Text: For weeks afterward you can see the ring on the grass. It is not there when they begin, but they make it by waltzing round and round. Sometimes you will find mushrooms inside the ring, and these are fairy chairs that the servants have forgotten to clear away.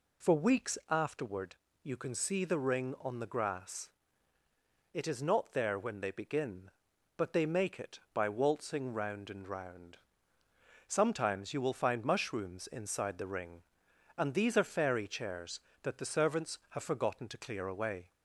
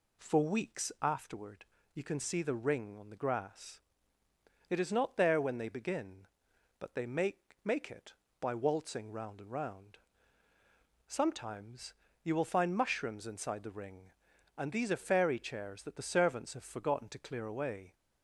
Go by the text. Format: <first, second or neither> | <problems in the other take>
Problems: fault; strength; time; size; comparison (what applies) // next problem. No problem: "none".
first | pauses between "afterward" and "you"; slight; at 1.6 s; 0.30 s long; slight in the first // says "make" twice; at 7.6 s // pauses between "Sometimes" and "you"; slight; at 11.9 s; 0.28 s long